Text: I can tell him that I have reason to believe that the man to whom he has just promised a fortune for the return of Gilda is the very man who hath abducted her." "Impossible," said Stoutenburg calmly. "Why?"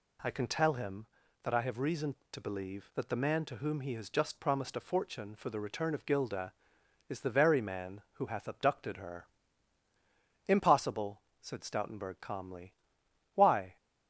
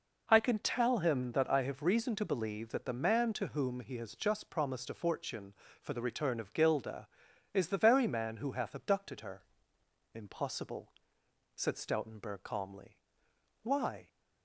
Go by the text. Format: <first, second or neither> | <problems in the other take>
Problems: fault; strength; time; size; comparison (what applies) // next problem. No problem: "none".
neither | none